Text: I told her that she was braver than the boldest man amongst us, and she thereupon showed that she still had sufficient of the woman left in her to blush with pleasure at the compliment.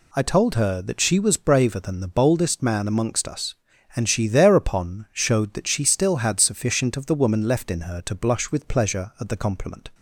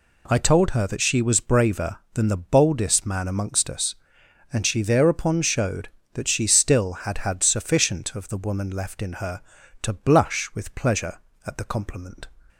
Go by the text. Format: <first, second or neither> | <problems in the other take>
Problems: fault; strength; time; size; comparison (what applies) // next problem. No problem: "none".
first | says "had" twice; at 7.1 s